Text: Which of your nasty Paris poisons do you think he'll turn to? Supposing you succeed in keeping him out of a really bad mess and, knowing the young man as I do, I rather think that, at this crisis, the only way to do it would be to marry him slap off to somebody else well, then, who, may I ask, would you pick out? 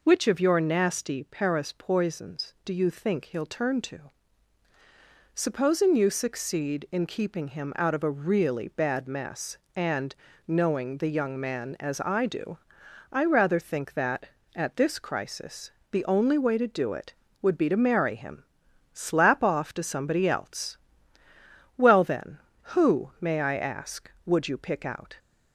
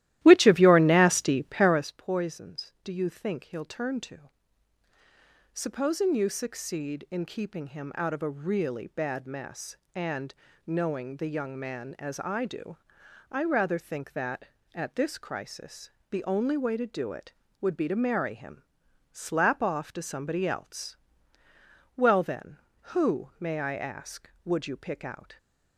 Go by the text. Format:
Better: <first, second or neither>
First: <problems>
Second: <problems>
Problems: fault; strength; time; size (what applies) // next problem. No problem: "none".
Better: first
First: pauses between "him" and "slap"; noticeable; at 18.4 s; 0.50 s long // pauses between "else" and "well"; at 20.7 s; 1.0 s long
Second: starts louder than the rest; strong; until 1.9 s; 15 dB // pauses between "him" and "slap"; noticeable; at 18.6 s; 0.50 s long // pauses between "else" and "well"; at 20.9 s; 1.0 s long